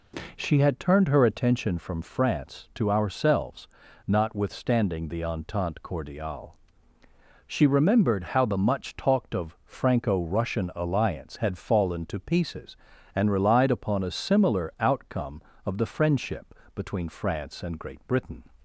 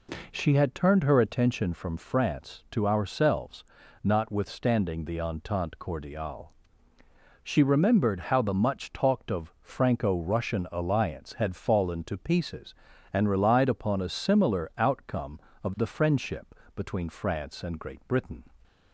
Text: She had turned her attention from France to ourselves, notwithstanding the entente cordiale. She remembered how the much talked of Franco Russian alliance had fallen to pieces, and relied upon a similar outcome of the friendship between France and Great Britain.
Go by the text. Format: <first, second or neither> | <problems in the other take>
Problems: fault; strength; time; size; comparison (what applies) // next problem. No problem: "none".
neither | pauses between "friendship" and "between"; slight; the same in both